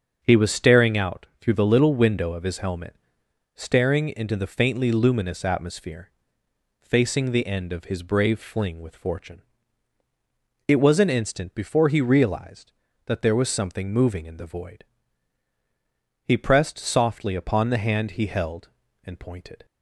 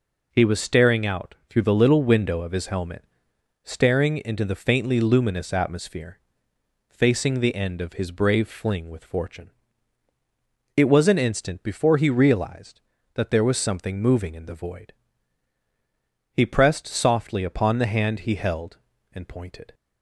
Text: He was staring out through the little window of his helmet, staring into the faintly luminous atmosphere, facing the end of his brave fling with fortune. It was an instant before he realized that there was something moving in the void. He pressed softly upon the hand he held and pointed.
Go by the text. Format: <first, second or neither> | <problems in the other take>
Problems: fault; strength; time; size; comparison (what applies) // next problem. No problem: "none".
second | starts louder than the rest; until 1.3 s; 7 dB // pauses between "out" and "through"; slight; at 1.2 s; 0.16 s long; slight in the second